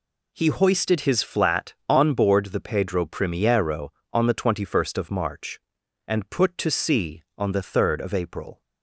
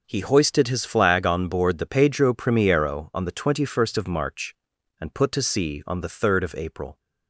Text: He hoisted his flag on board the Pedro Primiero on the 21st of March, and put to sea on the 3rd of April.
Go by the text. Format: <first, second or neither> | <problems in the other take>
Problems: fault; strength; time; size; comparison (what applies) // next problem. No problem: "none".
second | says "flat" for "flag"; at 1.2 s